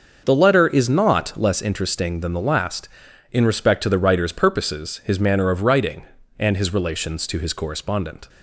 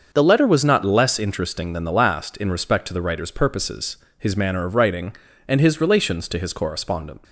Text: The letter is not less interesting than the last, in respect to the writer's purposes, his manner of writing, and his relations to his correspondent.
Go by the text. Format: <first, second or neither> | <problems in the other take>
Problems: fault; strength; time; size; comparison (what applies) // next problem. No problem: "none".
first | starts louder than the rest; until 1.1 s; 6.5 dB // says "was" for "is"; at 0.4 s